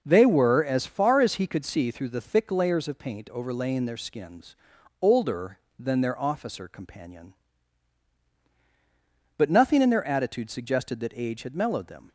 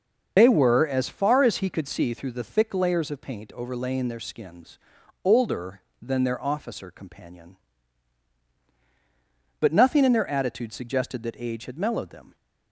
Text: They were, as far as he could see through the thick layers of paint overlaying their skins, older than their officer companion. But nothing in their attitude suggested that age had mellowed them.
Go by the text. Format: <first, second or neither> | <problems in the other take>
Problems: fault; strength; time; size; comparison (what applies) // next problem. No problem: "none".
first | loses the start of "They"; at 0.3 s; 95 ms // starts louder than the rest; until 1.3 s; 6 dB